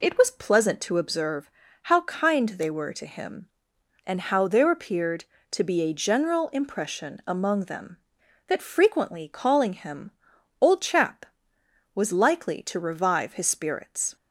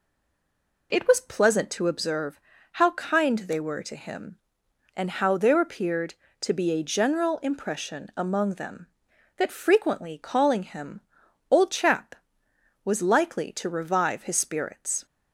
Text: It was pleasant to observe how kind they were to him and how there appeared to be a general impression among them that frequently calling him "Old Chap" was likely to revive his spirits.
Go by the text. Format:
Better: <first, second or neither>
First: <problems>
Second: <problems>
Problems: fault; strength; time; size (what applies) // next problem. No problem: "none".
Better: first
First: pauses between "observe" and "how"; slight; at 1.5 s; 0.32 s long // pauses between "him" and "Old"; noticeable; at 10.0 s; 0.50 s long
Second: stays silent before the first word; slight; until 0.9 s; 0.9 s long // pauses between "observe" and "how"; slight; at 2.4 s; 0.32 s long // pauses between "him" and "Old"; noticeable; at 10.9 s; 0.50 s long